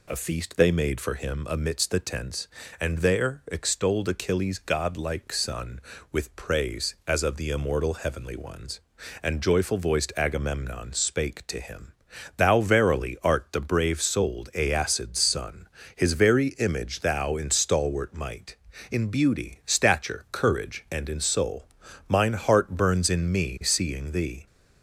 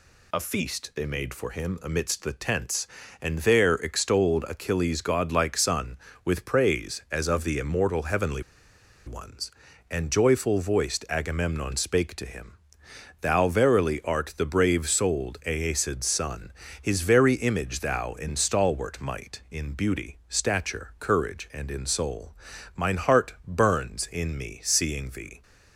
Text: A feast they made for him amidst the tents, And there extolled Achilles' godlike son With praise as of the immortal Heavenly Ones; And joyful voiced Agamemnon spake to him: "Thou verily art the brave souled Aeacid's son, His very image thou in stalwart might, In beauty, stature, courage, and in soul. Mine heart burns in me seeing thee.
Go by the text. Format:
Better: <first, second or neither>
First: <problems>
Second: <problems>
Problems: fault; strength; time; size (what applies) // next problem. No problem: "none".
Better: first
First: none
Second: pauses between "Heavenly" and "Ones"; noticeable; at 8.4 s; 0.63 s long